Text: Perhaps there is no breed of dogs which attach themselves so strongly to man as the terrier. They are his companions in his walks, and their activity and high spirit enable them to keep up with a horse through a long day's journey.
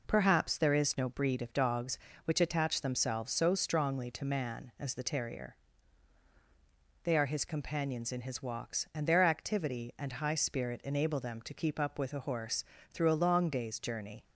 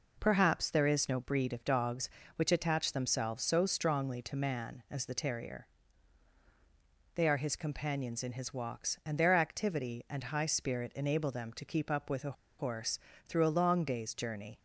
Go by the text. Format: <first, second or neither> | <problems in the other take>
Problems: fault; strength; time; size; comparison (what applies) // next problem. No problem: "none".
first | pauses between "a" and "horse"; slight; at 12.3 s; 0.26 s long // pauses between "horse" and "through"; slight; at 12.9 s; 0.30 s long; slight in the first